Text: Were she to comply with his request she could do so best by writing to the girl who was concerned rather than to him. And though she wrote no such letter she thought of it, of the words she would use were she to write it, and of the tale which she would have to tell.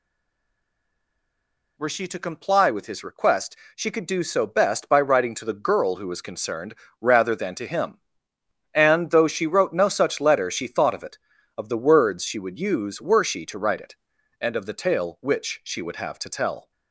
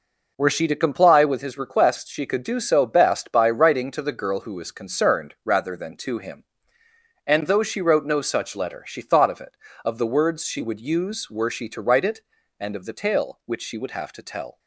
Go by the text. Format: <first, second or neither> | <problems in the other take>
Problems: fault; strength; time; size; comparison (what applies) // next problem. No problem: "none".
second | stays silent before the first word; noticeable; until 1.7 s; 1.7 s long // pauses between "request" and "she"; slight; at 3.5 s; 0.18 s long // pauses between "concerned" and "rather"; slight; at 6.7 s; 0.26 s long